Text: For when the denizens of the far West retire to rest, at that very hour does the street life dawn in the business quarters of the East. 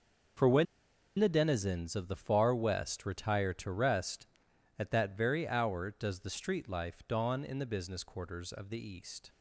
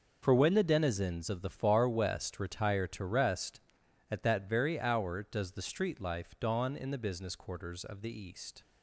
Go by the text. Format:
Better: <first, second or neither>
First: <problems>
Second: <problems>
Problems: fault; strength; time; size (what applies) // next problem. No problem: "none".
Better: second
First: starts louder than the rest; noticeable; until 1.9 s; 6 dB // pauses between "when" and "the"; noticeable; at 0.6 s; 0.53 s long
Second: starts louder than the rest; noticeable; until 1.2 s; 6 dB